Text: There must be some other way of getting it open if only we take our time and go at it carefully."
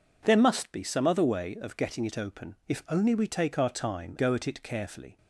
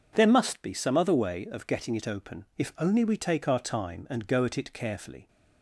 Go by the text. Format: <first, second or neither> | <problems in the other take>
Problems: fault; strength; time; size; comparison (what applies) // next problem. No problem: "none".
second | skips "and"; at 4.1 s